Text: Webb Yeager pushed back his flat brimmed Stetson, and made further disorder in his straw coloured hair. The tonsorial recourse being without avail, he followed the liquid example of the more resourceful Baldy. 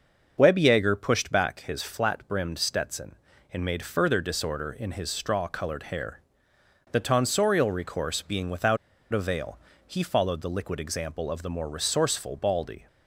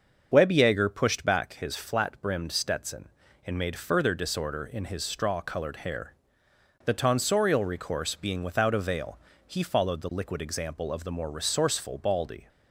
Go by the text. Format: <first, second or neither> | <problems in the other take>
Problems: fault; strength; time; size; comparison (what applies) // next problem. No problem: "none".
second | starts louder than the rest; until 1.3 s; 6.5 dB; also in the second // pauses between "without" and "avail"; slight; at 8.7 s; 0.35 s long